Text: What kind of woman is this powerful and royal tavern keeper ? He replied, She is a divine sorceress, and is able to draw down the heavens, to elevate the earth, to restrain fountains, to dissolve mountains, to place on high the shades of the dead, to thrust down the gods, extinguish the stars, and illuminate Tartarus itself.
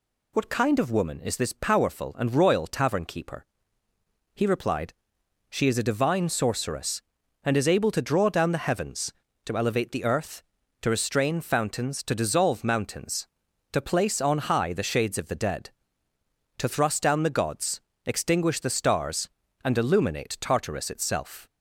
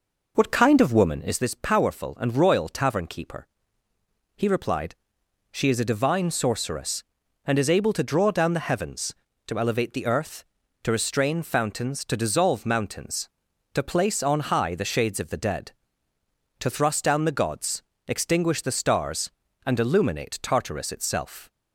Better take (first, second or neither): first